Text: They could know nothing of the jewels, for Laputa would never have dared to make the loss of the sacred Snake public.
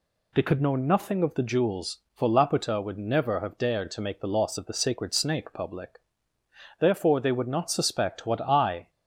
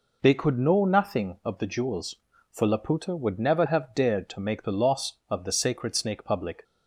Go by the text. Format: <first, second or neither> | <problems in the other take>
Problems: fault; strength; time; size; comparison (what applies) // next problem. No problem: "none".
second | goes on to say "Therefore they would not suspect what I"; strong; from 6.7 s on; 2.1 s long